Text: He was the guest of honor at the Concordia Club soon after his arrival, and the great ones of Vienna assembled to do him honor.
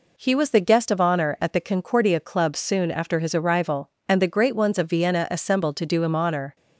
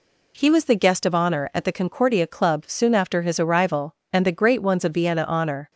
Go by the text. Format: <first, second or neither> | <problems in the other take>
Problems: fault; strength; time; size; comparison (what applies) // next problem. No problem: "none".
first | skips "assembled to do him"; at 5.2 s